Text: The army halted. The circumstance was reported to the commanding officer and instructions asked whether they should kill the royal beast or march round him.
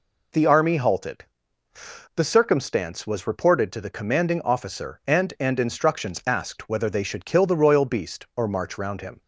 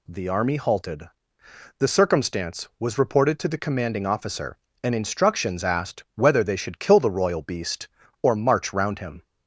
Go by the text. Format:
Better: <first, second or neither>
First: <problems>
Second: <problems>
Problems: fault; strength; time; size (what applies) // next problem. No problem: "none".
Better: second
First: says "and" twice; at 5.4 s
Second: none